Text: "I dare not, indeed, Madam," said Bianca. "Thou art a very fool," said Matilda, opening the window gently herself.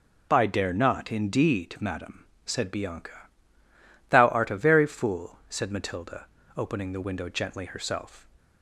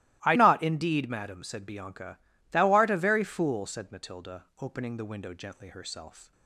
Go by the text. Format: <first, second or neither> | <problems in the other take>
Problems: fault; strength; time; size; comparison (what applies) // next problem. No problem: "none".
first | starts louder than the rest; strong; until 1.2 s; 18 dB // skips "dare"; at 0.3 s